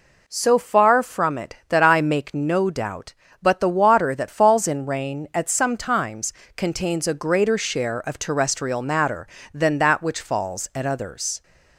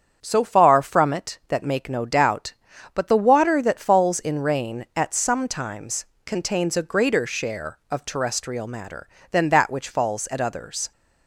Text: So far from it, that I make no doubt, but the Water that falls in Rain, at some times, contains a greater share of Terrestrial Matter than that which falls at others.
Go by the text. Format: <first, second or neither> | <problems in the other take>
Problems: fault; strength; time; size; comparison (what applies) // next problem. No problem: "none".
first | starts louder than the rest; strong; until 1.2 s; 7.5 dB // skips "I"; at 1.6 s